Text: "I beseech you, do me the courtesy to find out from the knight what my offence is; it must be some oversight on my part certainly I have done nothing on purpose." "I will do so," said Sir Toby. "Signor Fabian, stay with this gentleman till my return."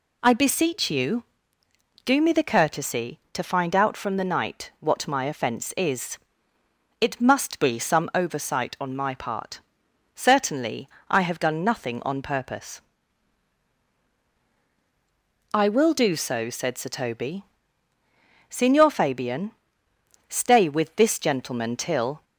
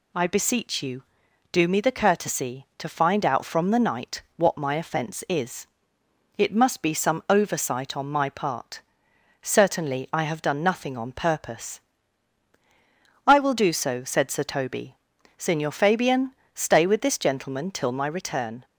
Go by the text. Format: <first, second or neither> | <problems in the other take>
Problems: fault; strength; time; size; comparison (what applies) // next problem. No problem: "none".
second | pauses between "part" and "certainly"; noticeable; at 9.5 s; 0.56 s long; noticeable in the second // pauses between "certainly" and "I"; slight; at 10.8 s; 0.18 s long // stops before "my return"; at 22.2 s